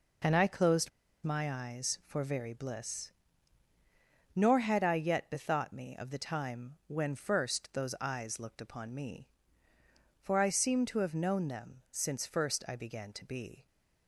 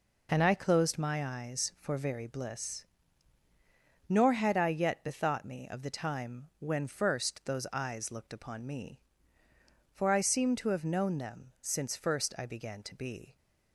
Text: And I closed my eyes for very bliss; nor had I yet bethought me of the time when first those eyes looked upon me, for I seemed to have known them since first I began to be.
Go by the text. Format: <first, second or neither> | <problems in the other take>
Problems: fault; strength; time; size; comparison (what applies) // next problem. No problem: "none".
second | pauses between "closed" and "my"; slight; at 0.8 s; 0.34 s long